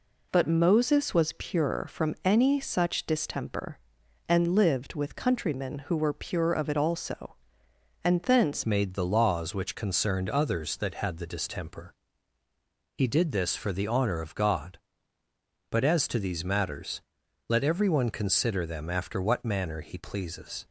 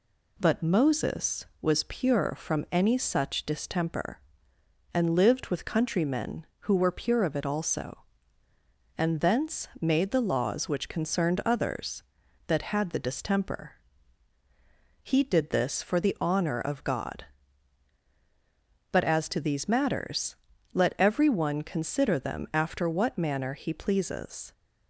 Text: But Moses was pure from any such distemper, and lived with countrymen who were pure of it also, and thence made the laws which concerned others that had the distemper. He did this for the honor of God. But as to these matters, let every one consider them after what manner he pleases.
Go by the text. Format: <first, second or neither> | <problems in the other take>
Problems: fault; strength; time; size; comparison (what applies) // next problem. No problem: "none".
second | changes voice at "made"; from 8.6 s on; 12.0 s long